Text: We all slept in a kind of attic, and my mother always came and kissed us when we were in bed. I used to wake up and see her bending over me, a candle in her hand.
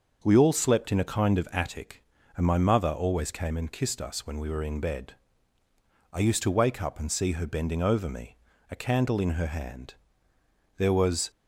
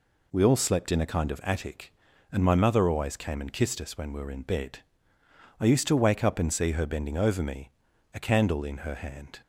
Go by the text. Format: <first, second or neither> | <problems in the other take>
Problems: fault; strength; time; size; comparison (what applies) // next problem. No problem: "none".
second | starts louder than the rest; until 1.2 s; 6.5 dB // goes on to say "There was"; from 10.7 s on; 0.54 s long